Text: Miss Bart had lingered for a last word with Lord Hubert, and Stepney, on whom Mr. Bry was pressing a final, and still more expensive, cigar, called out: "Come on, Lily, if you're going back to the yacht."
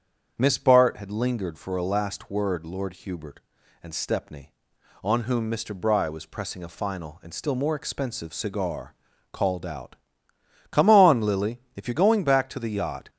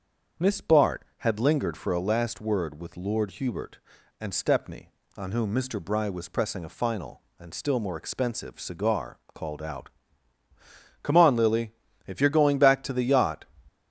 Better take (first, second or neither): second